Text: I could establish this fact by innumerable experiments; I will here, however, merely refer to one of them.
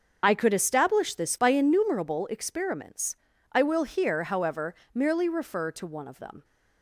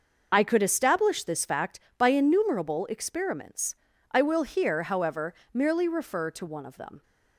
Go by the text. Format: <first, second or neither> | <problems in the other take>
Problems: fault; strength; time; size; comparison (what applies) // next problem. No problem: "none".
second | starts louder than the rest; until 1.2 s; 6.5 dB // skips "fact"; at 1.3 s